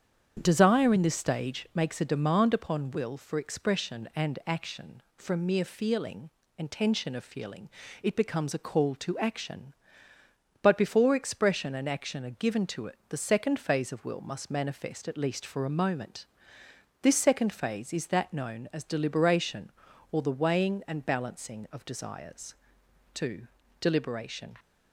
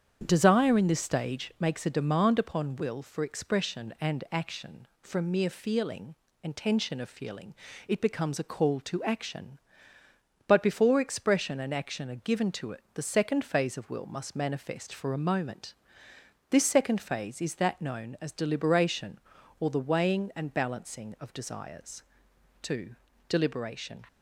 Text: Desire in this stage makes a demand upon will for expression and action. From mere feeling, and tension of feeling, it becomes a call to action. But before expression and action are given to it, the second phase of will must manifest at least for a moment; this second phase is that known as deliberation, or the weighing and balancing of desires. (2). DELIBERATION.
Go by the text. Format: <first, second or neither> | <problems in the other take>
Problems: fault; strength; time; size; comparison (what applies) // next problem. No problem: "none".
first | starts louder than the rest; strong; until 1.2 s; 8.5 dB; strong in the first // skips "at least"; at 14.9 s